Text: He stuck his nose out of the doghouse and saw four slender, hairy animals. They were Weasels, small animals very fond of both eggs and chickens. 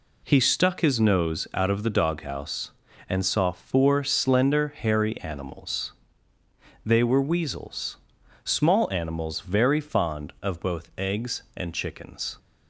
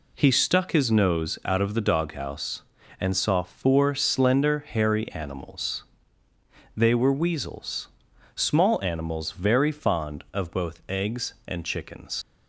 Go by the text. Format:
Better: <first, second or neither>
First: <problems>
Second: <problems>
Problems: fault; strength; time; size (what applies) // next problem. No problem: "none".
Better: first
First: none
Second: leaves "chickens" unfinished; at 12.2 s; 75 ms